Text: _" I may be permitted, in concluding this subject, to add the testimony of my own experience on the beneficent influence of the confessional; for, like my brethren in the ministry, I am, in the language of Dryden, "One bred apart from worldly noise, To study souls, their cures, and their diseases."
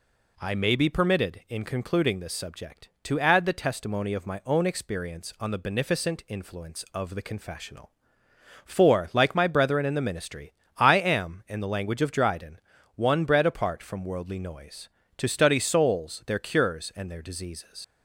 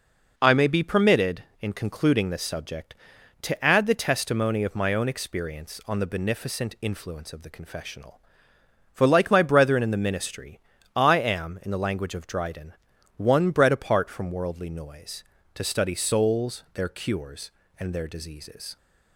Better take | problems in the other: second | leaves "diseases" unfinished; at 17.8 s; 100 ms

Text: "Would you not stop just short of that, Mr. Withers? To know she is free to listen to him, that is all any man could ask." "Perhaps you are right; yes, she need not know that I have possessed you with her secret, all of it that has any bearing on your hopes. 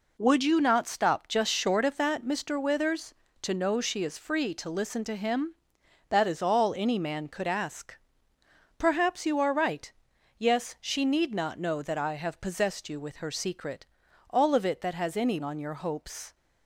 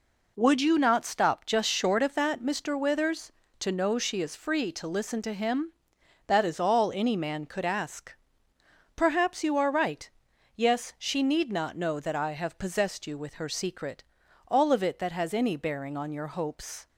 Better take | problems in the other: second | skips "bearing"; at 15.4 s

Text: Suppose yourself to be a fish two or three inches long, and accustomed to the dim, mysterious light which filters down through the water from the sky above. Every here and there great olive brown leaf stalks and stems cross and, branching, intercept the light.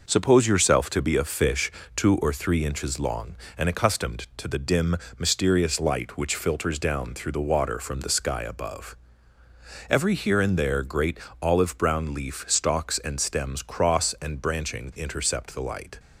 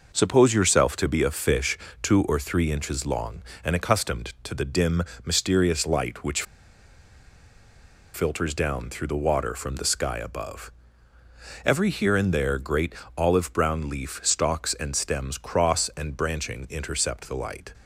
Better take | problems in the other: first | pauses between "fish" and "two"; slight; at 1.7 s; 0.24 s long; slight in the first // pauses between "which" and "filters"; strong; at 6.4 s; 1.7 s long // pauses between "great" and "olive"; slight; at 12.9 s; 0.24 s long; slight in the first

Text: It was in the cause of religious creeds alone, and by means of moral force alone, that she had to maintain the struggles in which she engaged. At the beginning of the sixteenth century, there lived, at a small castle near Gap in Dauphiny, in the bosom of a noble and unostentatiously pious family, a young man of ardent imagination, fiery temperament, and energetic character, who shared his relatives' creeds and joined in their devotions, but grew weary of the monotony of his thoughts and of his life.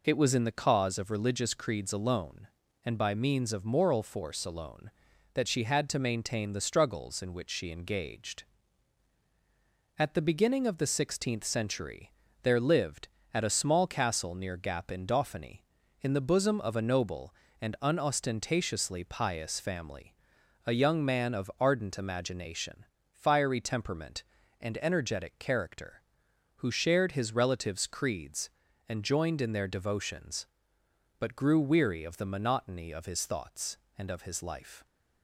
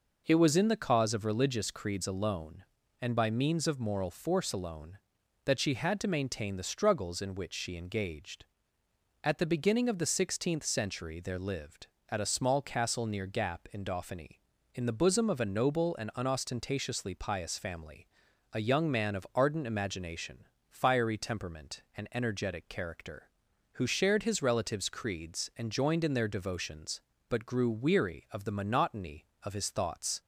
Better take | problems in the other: first | stops before "and of his life"; at 30.2 s

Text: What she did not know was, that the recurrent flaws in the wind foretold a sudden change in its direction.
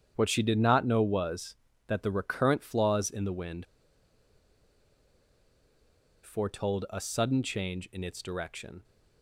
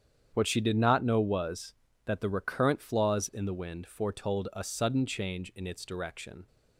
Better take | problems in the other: second | starts louder than the rest; strong; until 1.1 s; 8.5 dB; strong in the second // pauses between "wind" and "foretold"; strong; at 3.6 s; 2.5 s long

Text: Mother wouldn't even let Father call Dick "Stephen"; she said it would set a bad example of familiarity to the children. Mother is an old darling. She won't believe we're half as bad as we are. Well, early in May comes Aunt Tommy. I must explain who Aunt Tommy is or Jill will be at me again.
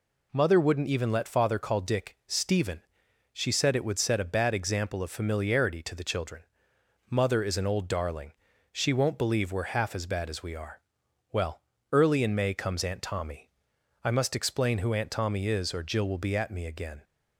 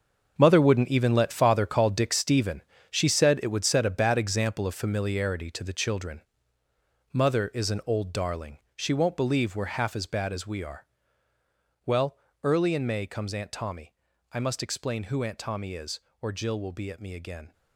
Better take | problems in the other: first | gets quieter; strong; throughout; 11.5 dB

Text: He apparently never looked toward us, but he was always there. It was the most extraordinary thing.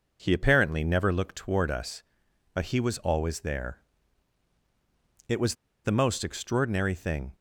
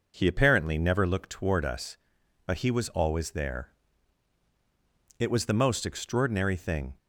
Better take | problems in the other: second | pauses between "was" and "the"; slight; at 5.5 s; 0.29 s long

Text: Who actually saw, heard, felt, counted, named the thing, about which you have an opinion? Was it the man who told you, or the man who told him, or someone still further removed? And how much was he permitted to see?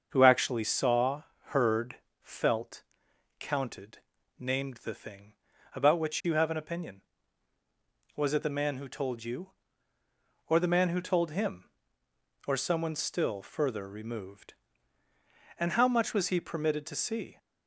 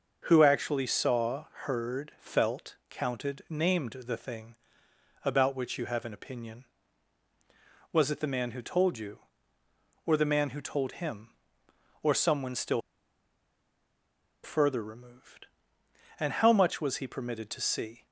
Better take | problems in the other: first | starts louder than the rest; noticeable; until 1.2 s; 6 dB; also in the first // pauses between "still" and "further"; strong; at 12.7 s; 1.6 s long

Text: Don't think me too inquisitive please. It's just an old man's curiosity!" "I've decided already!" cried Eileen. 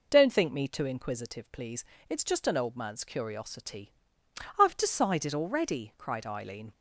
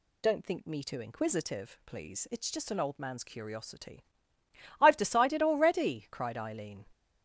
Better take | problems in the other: neither | none

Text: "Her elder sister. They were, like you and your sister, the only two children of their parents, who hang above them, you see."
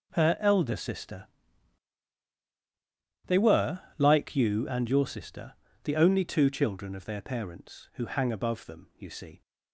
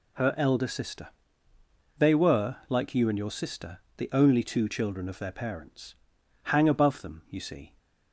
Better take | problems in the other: first | skips "who"; at 6.1 s

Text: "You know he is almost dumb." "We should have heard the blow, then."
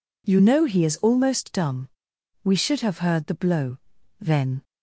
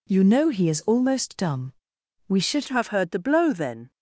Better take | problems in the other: first | changes voice at "have"; from 2.6 s on; 1.3 s long

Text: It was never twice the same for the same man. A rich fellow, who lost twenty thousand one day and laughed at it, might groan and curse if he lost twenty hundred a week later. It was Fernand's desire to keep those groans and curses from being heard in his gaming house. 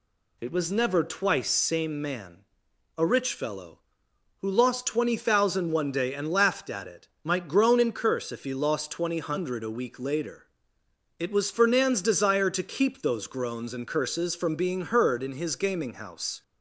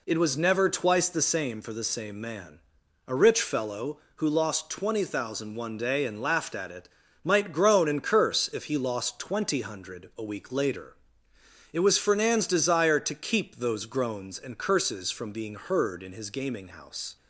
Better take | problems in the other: second | skips "the same for the"; at 1.5 s

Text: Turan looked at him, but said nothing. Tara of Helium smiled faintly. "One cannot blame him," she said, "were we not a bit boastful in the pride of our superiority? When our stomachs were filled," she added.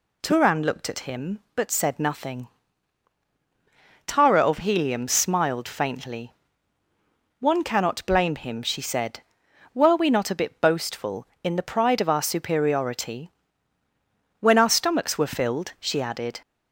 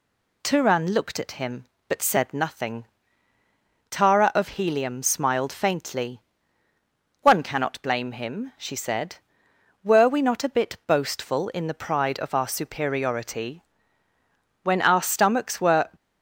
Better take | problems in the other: first | stops before "filled she added"; at 15.9 s

